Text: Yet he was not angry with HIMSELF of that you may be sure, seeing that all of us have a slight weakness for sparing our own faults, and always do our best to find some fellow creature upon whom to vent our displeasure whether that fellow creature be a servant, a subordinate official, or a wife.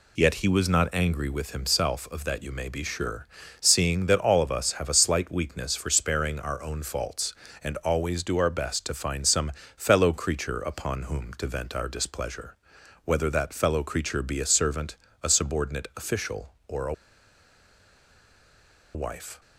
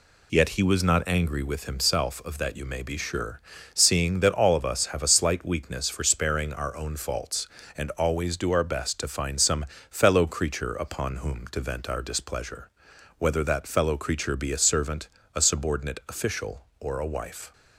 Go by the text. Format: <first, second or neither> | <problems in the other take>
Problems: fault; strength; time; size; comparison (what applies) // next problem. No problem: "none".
second | pauses between "some" and "fellow"; slight; at 9.5 s; 0.24 s long; slight in the second // pauses between "displeasure" and "whether"; noticeable; at 12.5 s; 0.48 s long; noticeable in the second // pauses between "a" and "wife"; strong; at 16.9 s; 2.0 s long